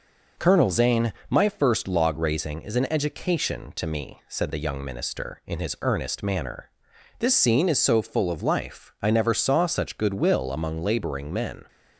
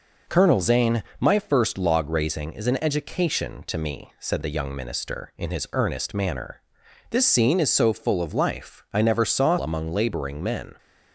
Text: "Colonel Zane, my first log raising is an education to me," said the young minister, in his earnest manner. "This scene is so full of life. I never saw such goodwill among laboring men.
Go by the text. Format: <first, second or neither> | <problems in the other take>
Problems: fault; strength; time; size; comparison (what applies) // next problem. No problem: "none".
first | skips "such goodwill"; at 9.5 s